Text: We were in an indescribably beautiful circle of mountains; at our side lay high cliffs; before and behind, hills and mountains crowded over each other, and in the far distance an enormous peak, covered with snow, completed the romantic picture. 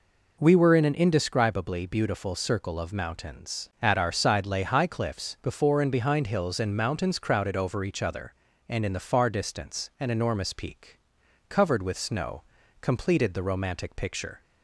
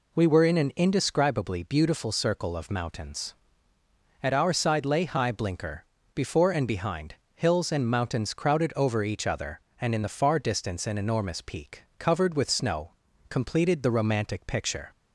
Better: first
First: none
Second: says "blinker" for "cliffs"; at 5.3 s

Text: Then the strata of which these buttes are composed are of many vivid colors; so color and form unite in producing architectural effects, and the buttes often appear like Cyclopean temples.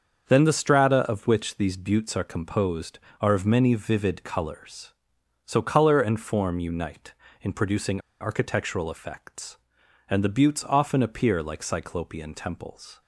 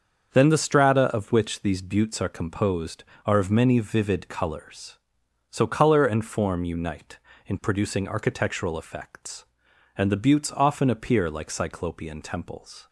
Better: second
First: starts louder than the rest; until 1.3 s; 7 dB // pauses between "producing" and "architectural"; slight; at 8.0 s; 0.19 s long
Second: starts louder than the rest; until 1.4 s; 7 dB

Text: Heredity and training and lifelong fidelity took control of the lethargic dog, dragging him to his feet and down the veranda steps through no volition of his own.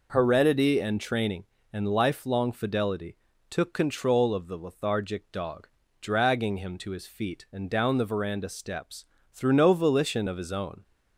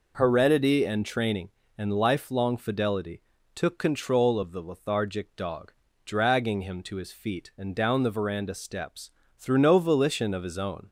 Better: neither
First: pauses between "fidelity" and "took"; slight; at 3.1 s; 0.34 s long // pauses between "steps" and "through"; slight; at 9.0 s; 0.28 s long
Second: pauses between "fidelity" and "took"; slight; at 3.1 s; 0.34 s long // pauses between "steps" and "through"; slight; at 9.0 s; 0.28 s long

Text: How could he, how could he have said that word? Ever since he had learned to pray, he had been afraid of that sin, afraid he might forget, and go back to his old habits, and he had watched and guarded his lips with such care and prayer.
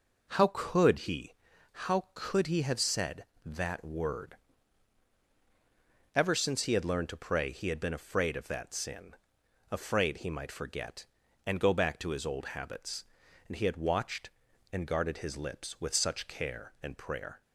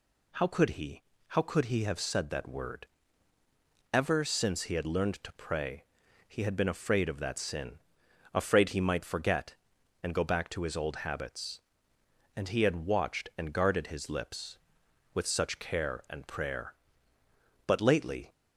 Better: first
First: none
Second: goes on to say "But lately"; noticeable; from 17.6 s on; 0.66 s long

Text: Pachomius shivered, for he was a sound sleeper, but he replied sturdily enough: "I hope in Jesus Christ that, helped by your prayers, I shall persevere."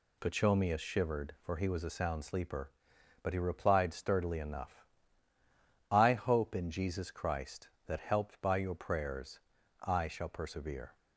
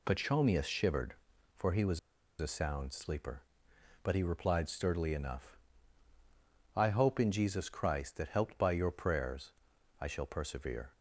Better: first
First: none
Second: pauses between "was" and "a"; at 1.9 s; 0.42 s long

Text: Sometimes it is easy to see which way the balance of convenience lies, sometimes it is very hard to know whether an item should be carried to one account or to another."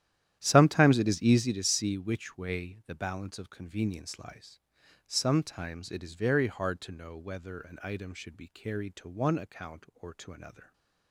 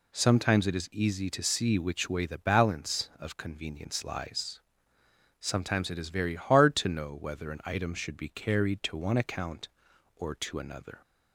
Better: second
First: starts louder than the rest; strong; until 1.5 s; 11.5 dB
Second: none

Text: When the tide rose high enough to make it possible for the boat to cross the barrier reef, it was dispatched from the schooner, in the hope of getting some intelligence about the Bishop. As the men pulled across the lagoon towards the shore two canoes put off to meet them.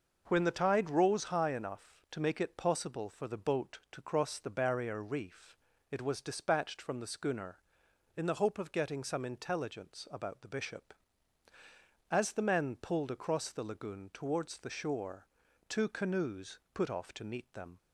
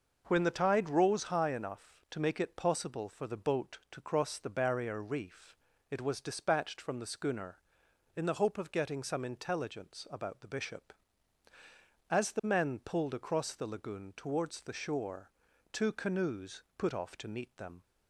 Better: neither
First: pauses between "shore" and "two"; at 15.2 s; 0.42 s long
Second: pauses between "shore" and "two"; at 15.2 s; 0.42 s long

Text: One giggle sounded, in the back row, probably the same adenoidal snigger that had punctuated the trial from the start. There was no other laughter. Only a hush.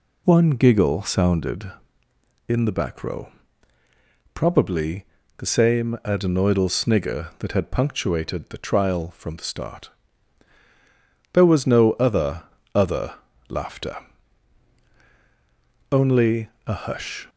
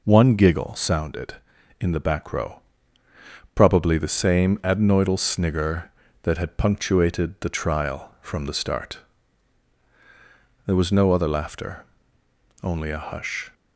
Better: second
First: pauses between "probably" and "the"; slight; at 5.0 s; 0.32 s long // says "other" twice; at 12.7 s // pauses between "Only" and "a"; slight; at 16.4 s; 0.16 s long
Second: none

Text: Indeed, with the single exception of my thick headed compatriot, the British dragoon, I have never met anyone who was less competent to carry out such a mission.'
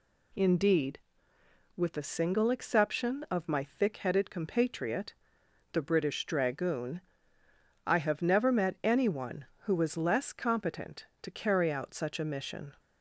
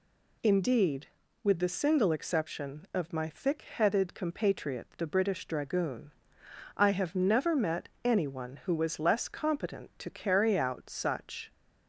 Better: first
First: none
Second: pauses between "met" and "anyone"; slight; at 7.8 s; 0.16 s long // stops before "a mission"; at 11.5 s

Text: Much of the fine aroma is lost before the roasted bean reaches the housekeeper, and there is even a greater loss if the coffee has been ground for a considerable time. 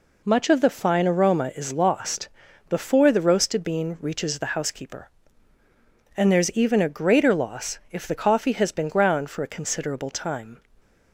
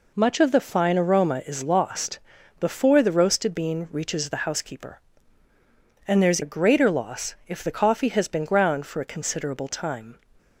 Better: first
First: pauses between "lost" and "before"; at 2.2 s; 0.40 s long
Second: pauses between "lost" and "before"; at 2.1 s; 0.40 s long // skips "even"; at 6.4 s

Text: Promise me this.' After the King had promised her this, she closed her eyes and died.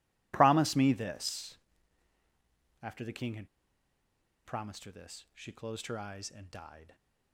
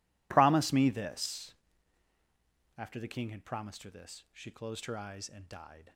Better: second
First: pauses between "had" and "promised"; noticeable; at 3.4 s; 0.96 s long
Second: none

